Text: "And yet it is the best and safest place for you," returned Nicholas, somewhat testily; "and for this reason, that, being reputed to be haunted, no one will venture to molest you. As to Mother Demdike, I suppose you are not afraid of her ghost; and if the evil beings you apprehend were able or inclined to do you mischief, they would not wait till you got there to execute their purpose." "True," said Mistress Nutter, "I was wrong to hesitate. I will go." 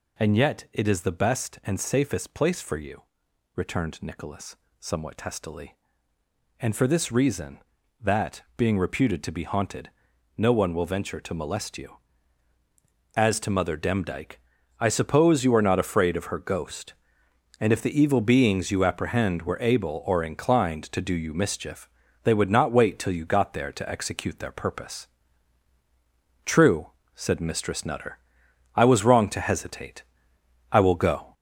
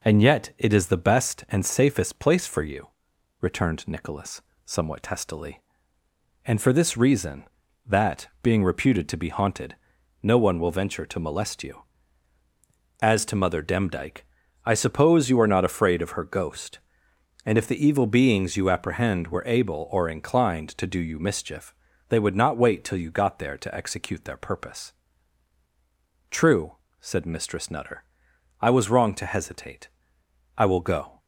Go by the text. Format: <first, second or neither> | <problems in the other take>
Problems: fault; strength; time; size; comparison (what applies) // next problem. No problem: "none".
second | gets louder; noticeable; throughout; 4 dB